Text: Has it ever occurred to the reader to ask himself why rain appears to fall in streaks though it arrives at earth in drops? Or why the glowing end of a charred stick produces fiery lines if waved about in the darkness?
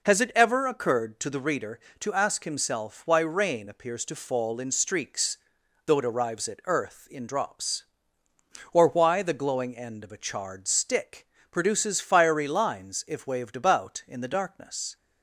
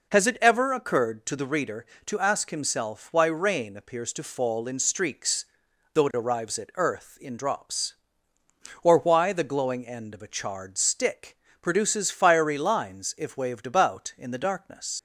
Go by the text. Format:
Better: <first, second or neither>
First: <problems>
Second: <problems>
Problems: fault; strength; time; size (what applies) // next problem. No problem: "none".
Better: first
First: pauses between "streaks" and "though"; noticeable; at 5.3 s; 0.48 s long // pauses between "stick" and "produces"; slight; at 11.2 s; 0.24 s long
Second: pauses between "streaks" and "though"; noticeable; at 5.4 s; 0.48 s long // pauses between "stick" and "produces"; slight; at 11.3 s; 0.24 s long // leaves "darkness" unfinished; at 14.9 s; 65 ms